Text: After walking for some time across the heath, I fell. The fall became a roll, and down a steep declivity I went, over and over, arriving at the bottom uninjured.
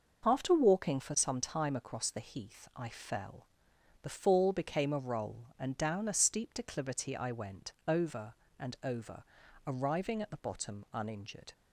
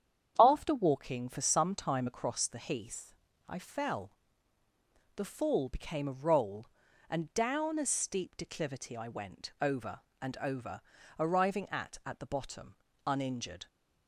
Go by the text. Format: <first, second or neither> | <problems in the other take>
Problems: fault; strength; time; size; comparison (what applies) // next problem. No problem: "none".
first | starts louder than the rest; strong; until 1.3 s; 8.5 dB // says "at" twice; at 12.0 s // pauses between "bottom" and "uninjured"; slight; at 12.7 s; 0.32 s long